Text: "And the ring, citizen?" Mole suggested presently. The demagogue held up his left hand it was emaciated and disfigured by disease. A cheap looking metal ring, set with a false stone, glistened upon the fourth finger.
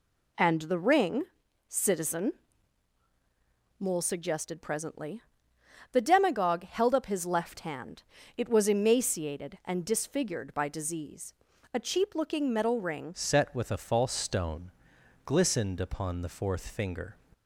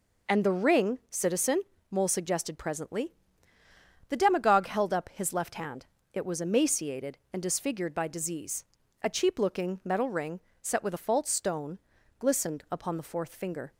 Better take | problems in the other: second | pauses between "hand" and "it"; slight; at 8.0 s; 0.32 s long; slight in the second // changes voice at "set"; from 13.1 s on; 4.0 s long

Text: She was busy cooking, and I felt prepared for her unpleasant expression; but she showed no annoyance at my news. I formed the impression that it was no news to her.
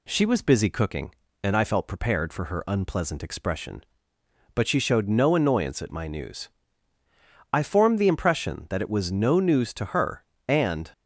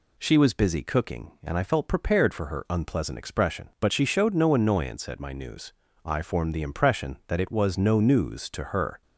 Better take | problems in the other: second | goes on to say "And"; slight; from 10.4 s on; 0.46 s long

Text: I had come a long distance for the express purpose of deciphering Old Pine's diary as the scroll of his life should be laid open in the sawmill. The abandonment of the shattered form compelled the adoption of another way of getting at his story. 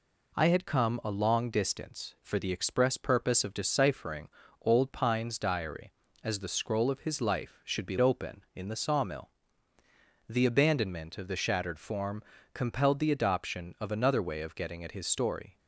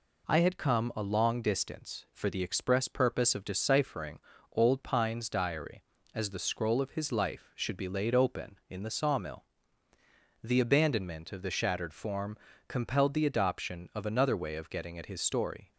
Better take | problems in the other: second | pauses between "deciphering" and "Old"; slight; at 4.2 s; 0.32 s long; slight in the second // skips "laid"; at 7.9 s // pauses between "form" and "compelled"; slight; at 12.2 s; 0.30 s long; slight in the second

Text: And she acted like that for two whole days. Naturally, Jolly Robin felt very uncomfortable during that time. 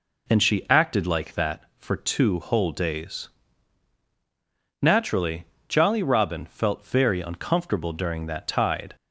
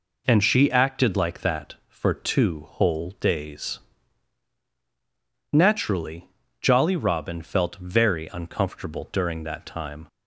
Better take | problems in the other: second | says "tide" for "time"; at 8.4 s

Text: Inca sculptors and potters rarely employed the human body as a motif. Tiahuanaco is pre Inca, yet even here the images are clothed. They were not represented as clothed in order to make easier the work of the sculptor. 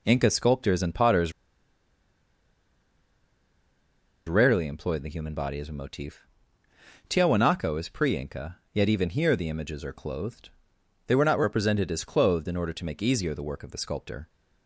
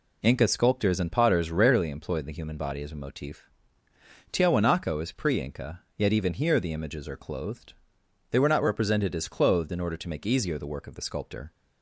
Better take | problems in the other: second | pauses between "potters" and "rarely"; strong; at 1.3 s; 2.9 s long

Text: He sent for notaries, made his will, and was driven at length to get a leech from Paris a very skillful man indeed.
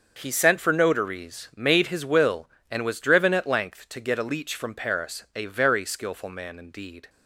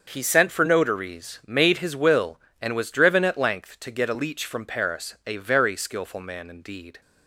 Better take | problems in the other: neither | starts louder than the rest; the same in both

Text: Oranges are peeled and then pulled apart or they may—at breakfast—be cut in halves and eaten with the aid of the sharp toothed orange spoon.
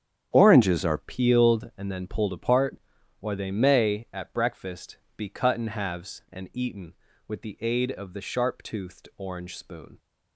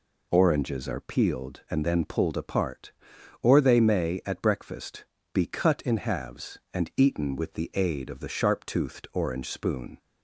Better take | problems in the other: second | starts louder than the rest; strong; until 1.3 s; 9 dB // changes voice at "peeled"; from 0.9 s on; 9.0 s long

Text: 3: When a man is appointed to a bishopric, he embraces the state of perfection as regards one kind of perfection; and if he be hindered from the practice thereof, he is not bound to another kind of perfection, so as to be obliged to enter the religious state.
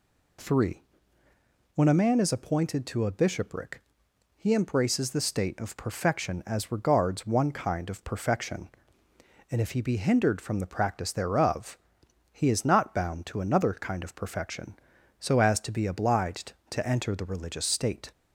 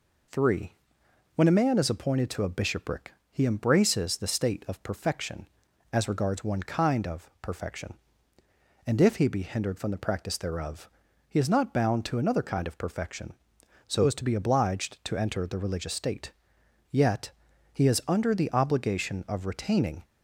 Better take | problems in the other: first | goes on to say "Yet he is under the obligation of retaining"; strong; from 16.9 s on; 3.1 s long

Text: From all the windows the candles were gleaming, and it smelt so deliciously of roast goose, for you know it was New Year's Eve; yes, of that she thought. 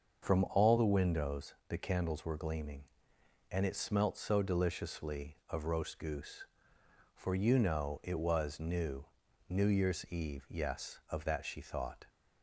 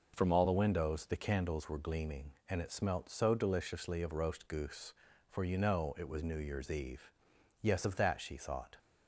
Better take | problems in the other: second | starts louder than the rest; until 1.3 s; 6.5 dB // says "New" twice; at 9.4 s

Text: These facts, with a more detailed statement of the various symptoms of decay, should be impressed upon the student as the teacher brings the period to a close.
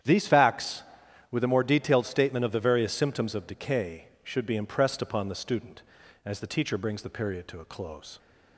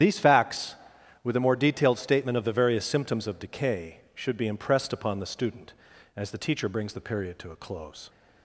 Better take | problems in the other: first | loses the start of "These"; at 0.0 s; 60 ms // starts louder than the rest; strong; until 1.4 s; 10 dB; strong in the first

